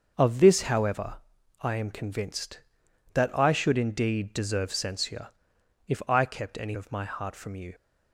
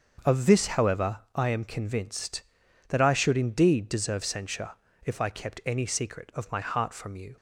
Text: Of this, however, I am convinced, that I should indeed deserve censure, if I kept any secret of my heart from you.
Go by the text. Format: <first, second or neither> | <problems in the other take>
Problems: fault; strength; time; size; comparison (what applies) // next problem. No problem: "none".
second | starts louder than the rest; until 1.1 s; 6.5 dB; also in the second // skips "secret"; at 6.7 s